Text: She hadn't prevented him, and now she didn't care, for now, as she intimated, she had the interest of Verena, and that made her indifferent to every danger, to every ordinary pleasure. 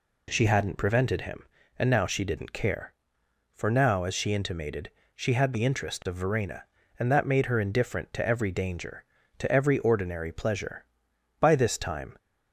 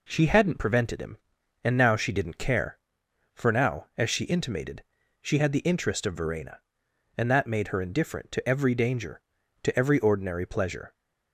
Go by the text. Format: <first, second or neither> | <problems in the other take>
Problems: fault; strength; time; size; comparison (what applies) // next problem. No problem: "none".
second | goes on to say "By this time"; noticeable; from 11.4 s on; 0.76 s long